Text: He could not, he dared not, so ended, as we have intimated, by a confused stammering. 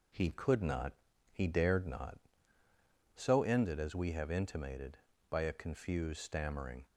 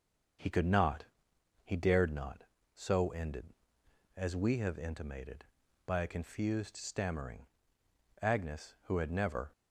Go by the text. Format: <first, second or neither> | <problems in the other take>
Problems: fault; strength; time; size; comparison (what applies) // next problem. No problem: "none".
first | starts louder than the rest; until 2.0 s; 6.5 dB // goes on to say "Agnes who had never"; noticeable; from 8.2 s on; 1.2 s long